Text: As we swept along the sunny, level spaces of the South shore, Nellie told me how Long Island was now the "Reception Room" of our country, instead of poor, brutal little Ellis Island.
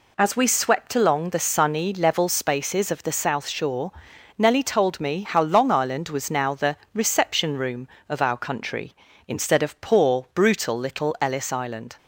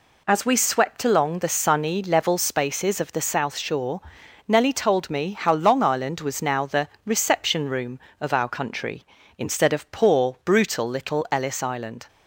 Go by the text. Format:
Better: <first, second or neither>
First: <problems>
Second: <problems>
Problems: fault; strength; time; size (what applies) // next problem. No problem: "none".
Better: neither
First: pauses between "the" and "Reception"; slight; at 6.7 s; 0.18 s long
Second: pauses between "the" and "Reception"; slight; at 6.8 s; 0.18 s long